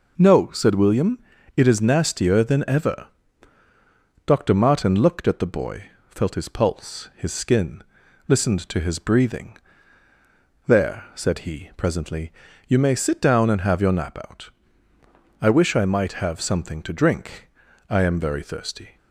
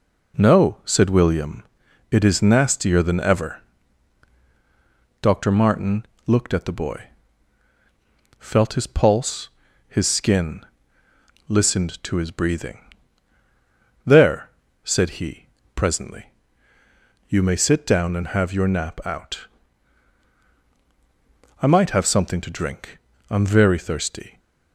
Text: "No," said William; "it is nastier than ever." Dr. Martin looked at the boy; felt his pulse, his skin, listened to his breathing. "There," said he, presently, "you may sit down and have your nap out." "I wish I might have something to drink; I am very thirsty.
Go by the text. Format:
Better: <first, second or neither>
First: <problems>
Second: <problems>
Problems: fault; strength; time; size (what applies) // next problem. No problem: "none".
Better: first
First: none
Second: pauses between "Martin" and "looked"; slight; at 6.0 s; 0.22 s long // skips "I wish"; at 20.5 s